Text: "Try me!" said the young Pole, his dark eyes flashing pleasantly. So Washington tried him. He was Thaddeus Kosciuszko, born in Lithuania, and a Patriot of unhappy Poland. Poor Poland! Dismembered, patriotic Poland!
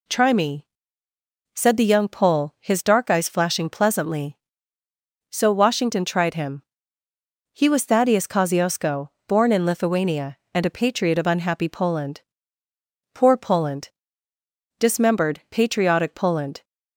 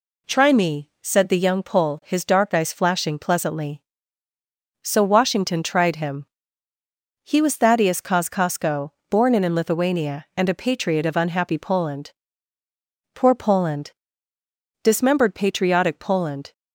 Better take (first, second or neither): first